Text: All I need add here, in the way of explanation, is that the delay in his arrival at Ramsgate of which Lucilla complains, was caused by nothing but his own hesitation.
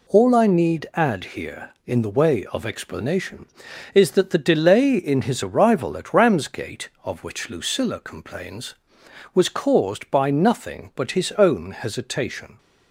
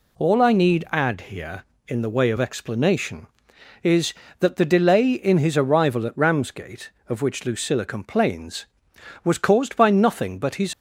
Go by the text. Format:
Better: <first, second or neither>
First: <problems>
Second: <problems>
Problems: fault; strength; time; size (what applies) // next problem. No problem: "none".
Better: first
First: none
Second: stops before "own hesitation"; at 10.7 s